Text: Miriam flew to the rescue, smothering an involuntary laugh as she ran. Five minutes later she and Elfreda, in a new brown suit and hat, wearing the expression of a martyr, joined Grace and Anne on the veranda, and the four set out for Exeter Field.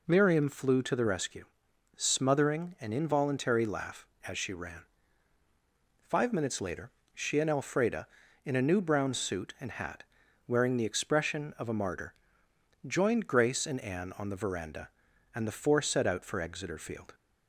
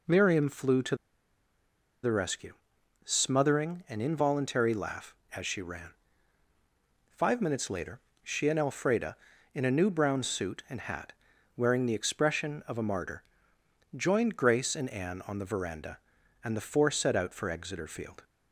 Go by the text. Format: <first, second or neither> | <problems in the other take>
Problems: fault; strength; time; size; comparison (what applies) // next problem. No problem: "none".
first | pauses between "to" and "the"; at 0.9 s; 1.0 s long // pauses between "later" and "she"; slight; at 7.9 s; 0.24 s long; slight in the first